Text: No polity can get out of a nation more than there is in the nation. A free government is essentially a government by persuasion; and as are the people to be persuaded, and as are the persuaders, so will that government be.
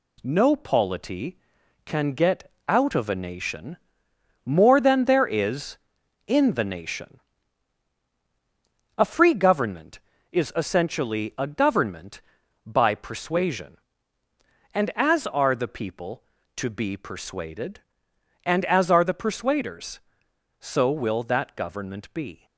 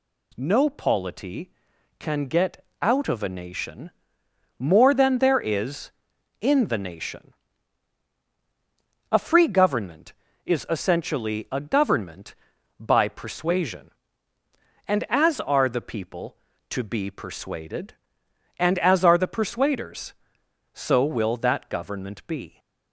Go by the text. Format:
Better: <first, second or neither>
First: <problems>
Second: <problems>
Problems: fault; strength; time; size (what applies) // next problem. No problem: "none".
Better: second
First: gets quieter; noticeable; throughout; 5 dB // pauses between "get" and "out"; slight; at 2.5 s; 0.16 s long // pauses between "nation" and "more"; noticeable; at 3.7 s; 0.68 s long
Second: pauses between "get" and "out"; slight; at 2.6 s; 0.16 s long // pauses between "nation" and "more"; noticeable; at 3.9 s; 0.68 s long